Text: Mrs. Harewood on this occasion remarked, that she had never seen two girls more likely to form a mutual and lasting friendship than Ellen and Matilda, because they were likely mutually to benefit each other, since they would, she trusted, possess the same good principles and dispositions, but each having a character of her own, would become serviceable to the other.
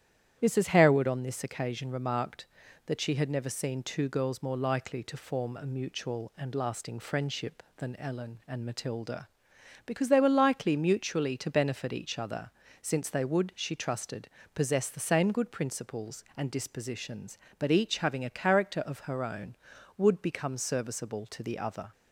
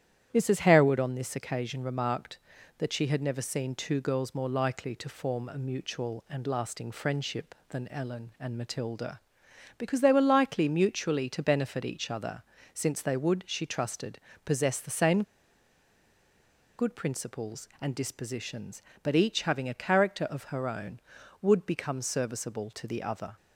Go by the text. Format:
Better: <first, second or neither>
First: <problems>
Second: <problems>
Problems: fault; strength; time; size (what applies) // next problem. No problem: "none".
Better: first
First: starts louder than the rest; strong; until 1.4 s; 10.5 dB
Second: starts louder than the rest; strong; until 1.3 s; 10.5 dB // pauses between "same" and "good"; strong; at 15.2 s; 1.5 s long